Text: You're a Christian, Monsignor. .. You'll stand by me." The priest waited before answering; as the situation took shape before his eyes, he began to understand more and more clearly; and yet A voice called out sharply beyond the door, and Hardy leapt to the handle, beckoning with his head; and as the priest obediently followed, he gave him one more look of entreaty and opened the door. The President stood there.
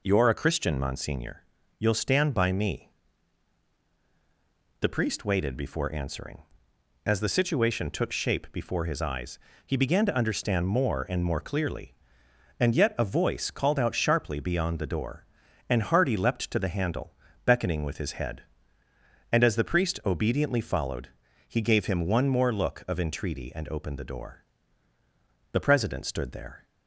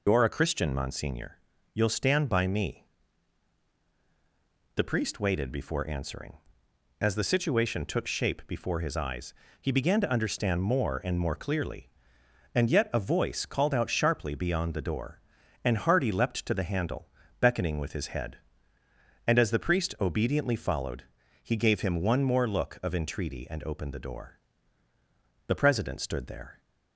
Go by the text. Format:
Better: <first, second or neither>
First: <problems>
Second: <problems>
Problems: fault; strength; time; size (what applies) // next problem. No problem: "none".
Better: first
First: none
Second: loses the start of "You're"; at 0.0 s; 70 ms